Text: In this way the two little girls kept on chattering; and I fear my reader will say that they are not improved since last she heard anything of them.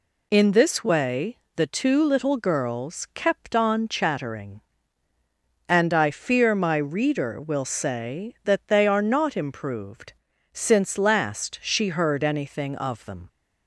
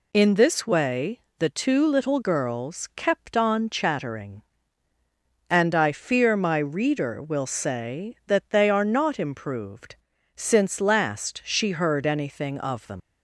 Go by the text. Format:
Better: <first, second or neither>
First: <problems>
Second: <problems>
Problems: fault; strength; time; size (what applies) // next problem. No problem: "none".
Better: first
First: pauses between "way" and "the"; slight; at 1.3 s; 0.18 s long // pauses between "improved" and "since"; at 10.1 s; 0.40 s long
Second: pauses between "way" and "the"; slight; at 1.1 s; 0.18 s long // pauses between "improved" and "since"; at 9.9 s; 0.40 s long // leaves "them" unfinished; at 13.0 s; 90 ms